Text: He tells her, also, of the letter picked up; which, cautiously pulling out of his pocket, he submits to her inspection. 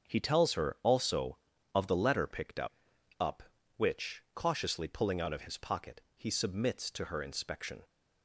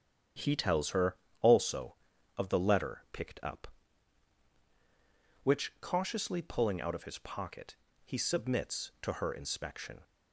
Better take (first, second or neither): second